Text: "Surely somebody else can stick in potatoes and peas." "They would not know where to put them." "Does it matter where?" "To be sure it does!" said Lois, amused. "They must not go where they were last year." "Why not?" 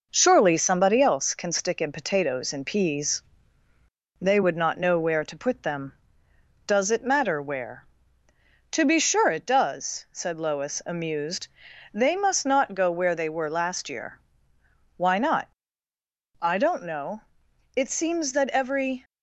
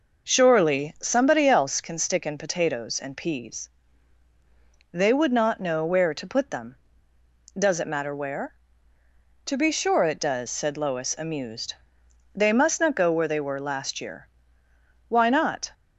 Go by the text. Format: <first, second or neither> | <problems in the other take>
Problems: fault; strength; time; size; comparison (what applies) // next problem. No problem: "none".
second | goes on to say "I don't know It seems that every"; strong; from 16.3 s on; 2.6 s long